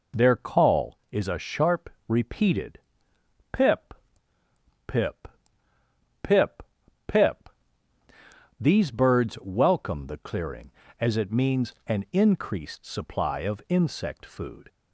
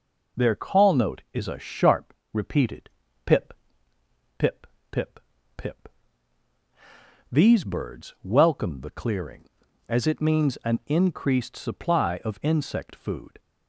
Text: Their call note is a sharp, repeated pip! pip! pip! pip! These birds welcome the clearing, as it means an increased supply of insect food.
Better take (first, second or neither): second